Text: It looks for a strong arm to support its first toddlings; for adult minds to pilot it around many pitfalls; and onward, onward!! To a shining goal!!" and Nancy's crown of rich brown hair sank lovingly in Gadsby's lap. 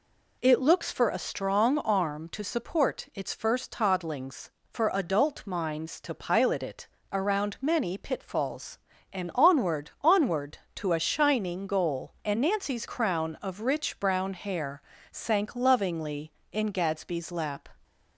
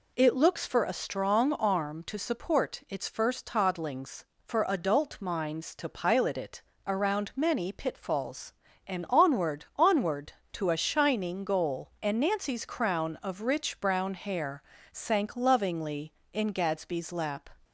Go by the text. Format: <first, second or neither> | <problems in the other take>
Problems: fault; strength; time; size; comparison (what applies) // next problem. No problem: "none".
neither | pauses between "it" and "around"; slight; the same in both // pauses between "hair" and "sank"; slight; the same in both